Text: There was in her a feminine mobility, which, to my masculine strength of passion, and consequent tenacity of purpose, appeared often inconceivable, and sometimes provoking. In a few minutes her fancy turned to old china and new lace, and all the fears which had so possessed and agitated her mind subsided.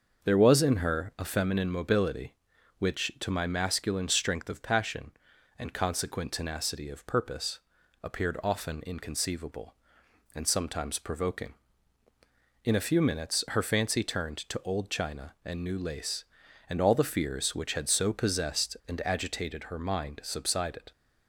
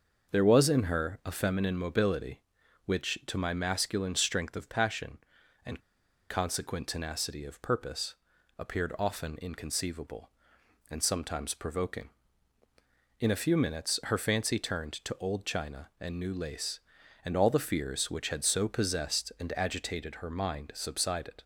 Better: first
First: starts louder than the rest; until 1.3 s; 6.5 dB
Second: starts louder than the rest; until 1.3 s; 6.5 dB // pauses between "and" and "consequent"; noticeable; at 5.7 s; 0.49 s long

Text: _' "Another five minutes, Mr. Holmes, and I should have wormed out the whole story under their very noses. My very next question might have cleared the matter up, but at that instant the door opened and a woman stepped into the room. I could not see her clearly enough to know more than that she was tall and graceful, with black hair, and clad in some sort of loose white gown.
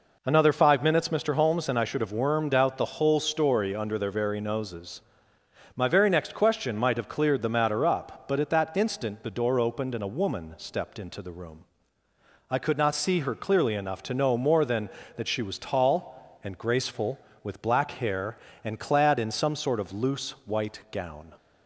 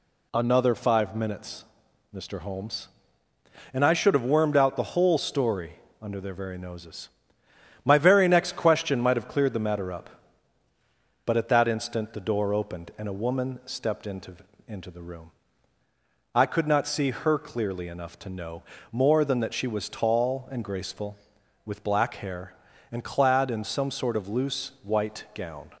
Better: first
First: none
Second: pauses between "story" and "under"; slight; at 5.7 s; 0.28 s long // says "into" twice; at 14.6 s // pauses between "know" and "more"; slight; at 18.6 s; 0.30 s long

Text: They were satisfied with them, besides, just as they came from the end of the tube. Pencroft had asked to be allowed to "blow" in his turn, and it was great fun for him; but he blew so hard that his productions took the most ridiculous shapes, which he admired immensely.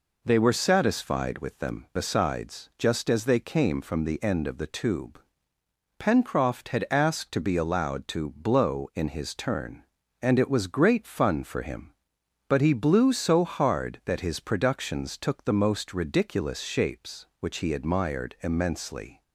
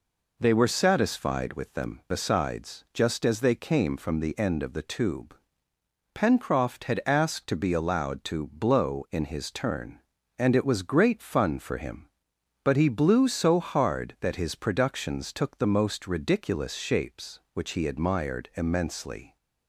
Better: neither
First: none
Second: none

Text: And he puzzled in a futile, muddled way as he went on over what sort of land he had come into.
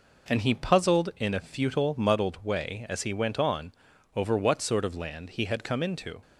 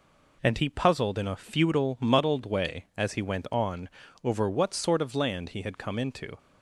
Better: neither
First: pauses between "on" and "over"; at 3.7 s; 0.44 s long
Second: pauses between "on" and "over"; slight; at 3.8 s; 0.34 s long

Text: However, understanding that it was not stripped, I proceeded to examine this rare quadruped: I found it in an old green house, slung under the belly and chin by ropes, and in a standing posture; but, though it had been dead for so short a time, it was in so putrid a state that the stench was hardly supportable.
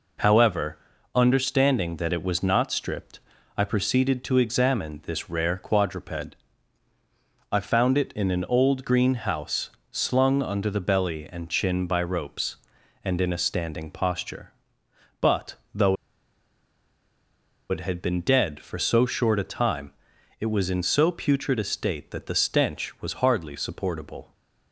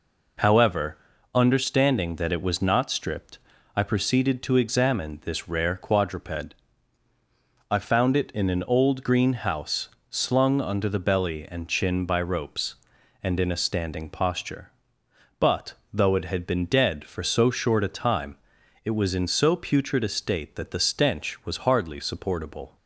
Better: second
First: pauses between "though" and "it"; strong; at 15.9 s; 1.7 s long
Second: none

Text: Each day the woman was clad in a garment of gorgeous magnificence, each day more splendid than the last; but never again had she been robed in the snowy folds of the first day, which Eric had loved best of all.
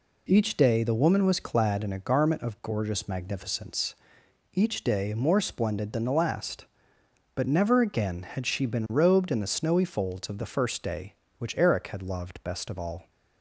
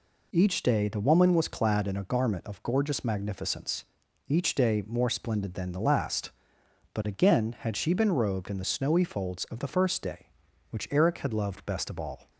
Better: first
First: none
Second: skips "never"; at 7.0 s

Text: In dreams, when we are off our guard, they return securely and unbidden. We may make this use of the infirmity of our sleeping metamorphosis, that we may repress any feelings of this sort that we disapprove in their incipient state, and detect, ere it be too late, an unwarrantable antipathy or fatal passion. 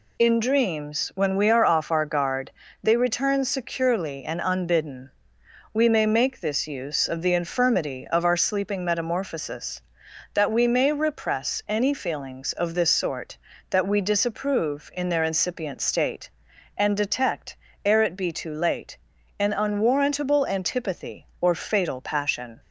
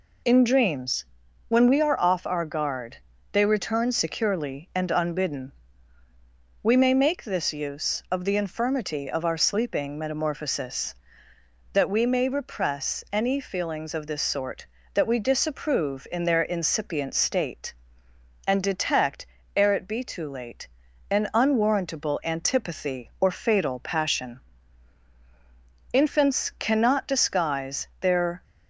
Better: first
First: none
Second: goes on to say "Infants cannot disguise their"; strong; from 25.9 s on; 2.5 s long

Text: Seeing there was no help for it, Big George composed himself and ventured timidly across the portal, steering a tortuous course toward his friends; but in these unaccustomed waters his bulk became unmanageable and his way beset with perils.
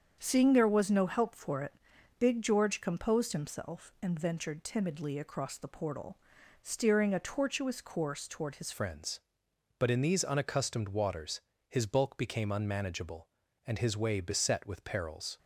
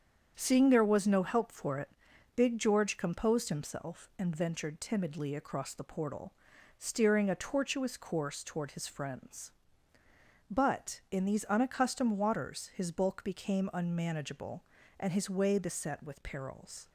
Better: second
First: starts louder than the rest; strong; until 1.2 s; 7.5 dB // changes voice at "friends"; from 8.7 s on; 6.6 s long // pauses between "waters" and "his"; slight; at 11.4 s; 0.26 s long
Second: starts louder than the rest; strong; until 1.3 s; 7.5 dB

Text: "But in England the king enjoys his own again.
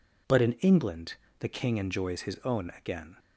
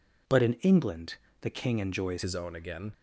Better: first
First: pauses between "England" and "the"; slight; at 1.1 s; 0.23 s long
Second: pauses between "England" and "the"; slight; at 1.1 s; 0.24 s long // changes voice at "his"; from 2.2 s on; 0.7 s long

